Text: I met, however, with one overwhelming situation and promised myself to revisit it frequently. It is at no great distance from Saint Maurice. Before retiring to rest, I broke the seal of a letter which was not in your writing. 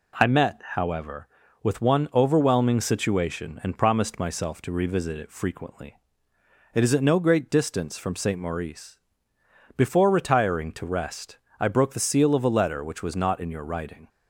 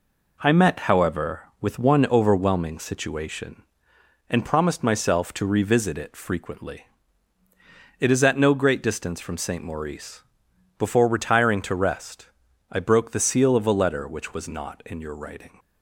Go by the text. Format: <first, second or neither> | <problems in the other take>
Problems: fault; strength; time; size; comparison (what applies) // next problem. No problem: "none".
neither | none